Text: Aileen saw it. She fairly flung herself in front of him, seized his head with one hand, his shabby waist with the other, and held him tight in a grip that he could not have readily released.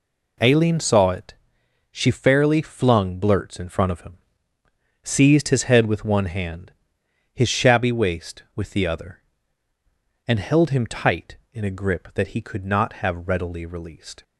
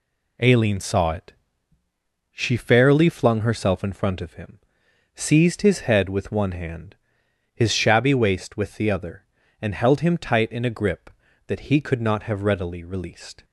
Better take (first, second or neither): second